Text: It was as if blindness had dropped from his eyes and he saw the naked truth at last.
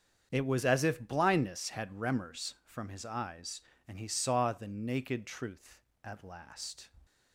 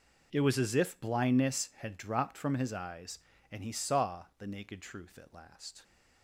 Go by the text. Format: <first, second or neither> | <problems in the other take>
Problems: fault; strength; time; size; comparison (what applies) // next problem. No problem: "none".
second | starts louder than the rest; strong; until 1.3 s; 7.5 dB // says "remors" for "dropped"; at 1.8 s